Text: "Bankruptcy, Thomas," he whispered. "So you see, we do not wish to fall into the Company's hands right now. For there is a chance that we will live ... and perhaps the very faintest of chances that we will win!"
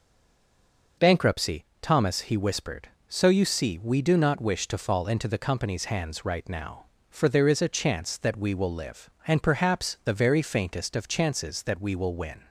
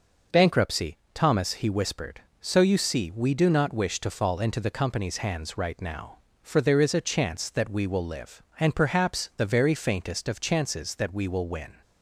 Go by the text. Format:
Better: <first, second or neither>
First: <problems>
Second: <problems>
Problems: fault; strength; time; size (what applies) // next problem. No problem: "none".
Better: second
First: stays silent before the first word; until 0.9 s; 0.9 s long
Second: none